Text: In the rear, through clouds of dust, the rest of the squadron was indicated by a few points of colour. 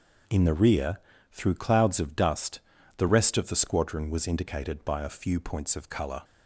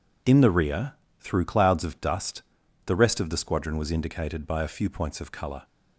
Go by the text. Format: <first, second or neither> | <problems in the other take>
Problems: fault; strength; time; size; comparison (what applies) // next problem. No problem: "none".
neither | none